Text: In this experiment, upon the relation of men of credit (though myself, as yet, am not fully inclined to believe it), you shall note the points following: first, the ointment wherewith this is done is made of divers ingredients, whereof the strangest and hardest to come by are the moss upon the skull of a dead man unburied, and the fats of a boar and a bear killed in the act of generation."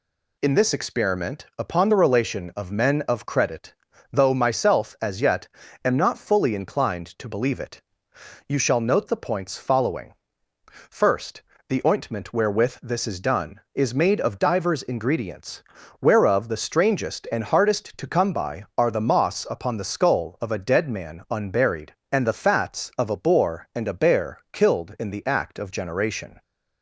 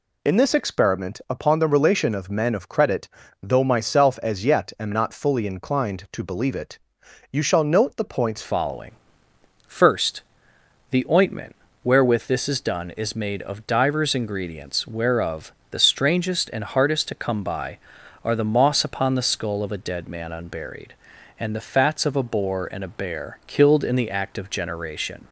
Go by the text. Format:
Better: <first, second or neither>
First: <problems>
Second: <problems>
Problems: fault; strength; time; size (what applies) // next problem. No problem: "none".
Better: first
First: none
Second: changes voice at "following"; from 8.4 s on; 16.8 s long // pauses between "ointment" and "wherewith"; slight; at 11.5 s; 0.30 s long // pauses between "whereof" and "the"; slight; at 15.5 s; 0.18 s long